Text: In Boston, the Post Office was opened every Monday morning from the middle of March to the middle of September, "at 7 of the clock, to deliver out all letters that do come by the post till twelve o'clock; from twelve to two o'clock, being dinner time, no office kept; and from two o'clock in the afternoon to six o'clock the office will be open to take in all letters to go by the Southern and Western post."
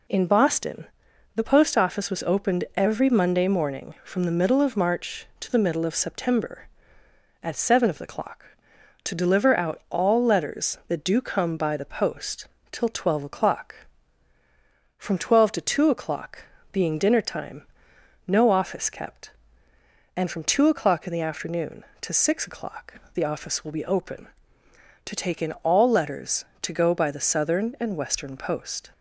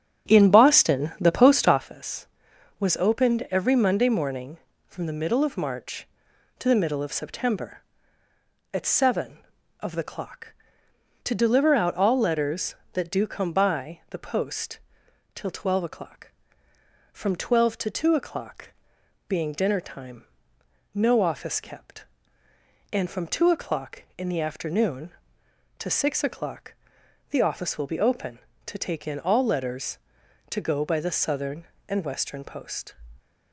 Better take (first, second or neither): first